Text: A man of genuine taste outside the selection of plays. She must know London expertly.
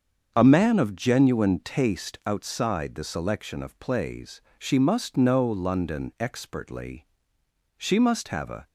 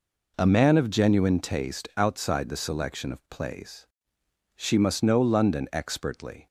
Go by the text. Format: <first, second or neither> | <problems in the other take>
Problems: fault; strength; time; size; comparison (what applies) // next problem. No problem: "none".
second | starts louder than the rest; until 1.3 s; 7 dB // goes on to say "She must have a"; noticeable; from 7.7 s on; 0.90 s long